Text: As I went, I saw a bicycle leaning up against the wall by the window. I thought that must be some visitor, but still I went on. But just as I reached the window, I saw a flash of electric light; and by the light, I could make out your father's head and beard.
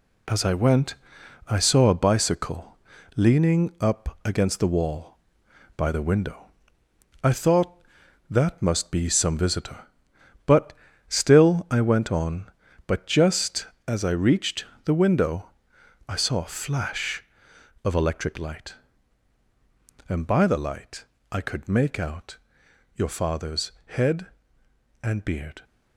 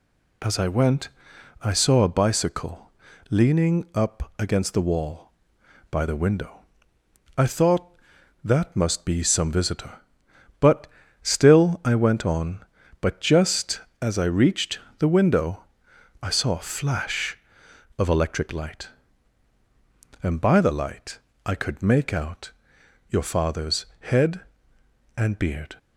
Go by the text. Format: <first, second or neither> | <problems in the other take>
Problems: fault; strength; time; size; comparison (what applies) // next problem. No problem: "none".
second | gets quieter; noticeable; throughout; 5.5 dB // pauses between "bicycle" and "leaning"; at 2.7 s; 0.38 s long; also in the second // pauses between "but" and "still"; slight; at 10.7 s; 0.36 s long; slight in the second // pauses between "reached" and "the"; slight; at 14.6 s; 0.20 s long; slight in the second // pauses between "out" and "your"; noticeable; at 22.3 s; 0.58 s long; noticeable in the second